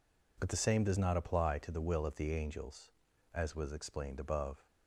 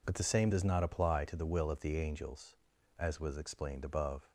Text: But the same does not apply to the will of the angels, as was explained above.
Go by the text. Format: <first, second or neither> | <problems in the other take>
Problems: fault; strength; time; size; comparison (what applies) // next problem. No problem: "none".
neither | none